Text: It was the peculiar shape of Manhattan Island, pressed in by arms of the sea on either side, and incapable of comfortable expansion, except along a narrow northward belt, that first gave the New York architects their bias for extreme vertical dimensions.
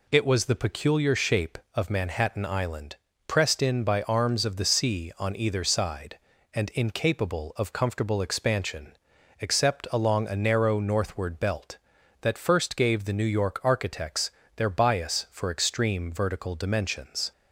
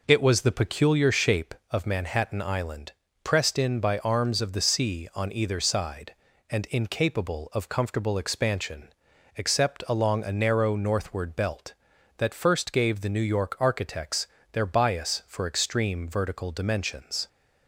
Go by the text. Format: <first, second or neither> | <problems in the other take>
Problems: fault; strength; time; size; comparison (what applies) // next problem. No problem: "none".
first | starts louder than the rest; noticeable; until 1.4 s; 5 dB // pauses between "architects" and "their"; slight; at 14.2 s; 0.24 s long; slight in the first